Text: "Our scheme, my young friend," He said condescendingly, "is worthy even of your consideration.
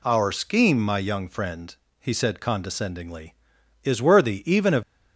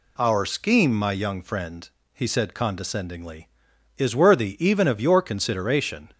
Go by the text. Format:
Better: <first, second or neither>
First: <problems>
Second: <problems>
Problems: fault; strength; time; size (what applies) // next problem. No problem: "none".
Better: second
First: stops before "your consideration"; at 4.8 s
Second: none